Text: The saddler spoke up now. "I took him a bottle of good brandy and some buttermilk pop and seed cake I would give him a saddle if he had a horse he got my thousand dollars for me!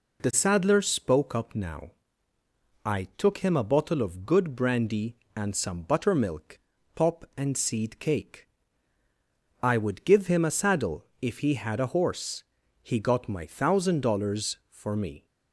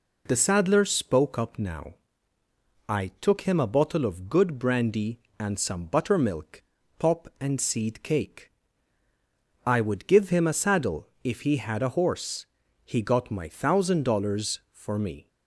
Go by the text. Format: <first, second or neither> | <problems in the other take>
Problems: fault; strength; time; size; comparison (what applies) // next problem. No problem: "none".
neither | pauses between "buttermilk" and "pop"; slight; the same in both // pauses between "cake" and "I"; the same in both // pauses between "saddle" and "if"; slight; the same in both // pauses between "horse" and "he"; the same in both